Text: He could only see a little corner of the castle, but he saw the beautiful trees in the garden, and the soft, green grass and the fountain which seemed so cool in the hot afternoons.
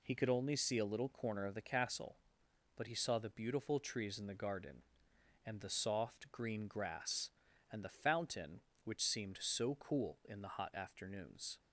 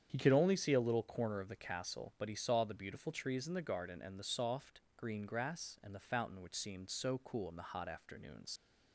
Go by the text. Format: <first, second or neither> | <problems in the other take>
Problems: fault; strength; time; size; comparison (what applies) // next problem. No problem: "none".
first | starts louder than the rest; strong; until 1.1 s; 8.5 dB // leaves "afternoons" unfinished; at 8.5 s; 70 ms